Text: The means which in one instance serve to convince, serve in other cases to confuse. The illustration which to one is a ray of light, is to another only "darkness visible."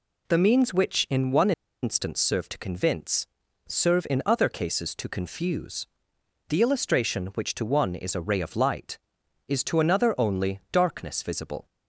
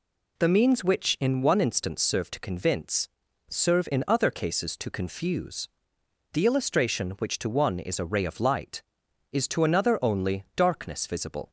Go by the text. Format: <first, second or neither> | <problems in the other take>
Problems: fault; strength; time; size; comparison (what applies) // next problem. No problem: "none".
second | pauses between "one" and "instance"; slight; at 1.5 s; 0.31 s long